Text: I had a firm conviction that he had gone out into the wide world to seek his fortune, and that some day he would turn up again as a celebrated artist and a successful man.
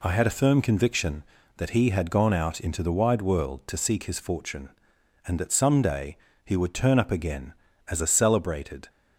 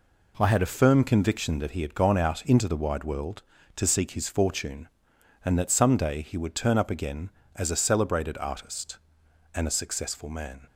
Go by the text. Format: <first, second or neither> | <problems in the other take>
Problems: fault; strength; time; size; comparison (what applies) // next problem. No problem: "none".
second | pauses between "day" and "he"; slight; at 6.1 s; 0.28 s long // stops before "artist and a successful man"; at 8.8 s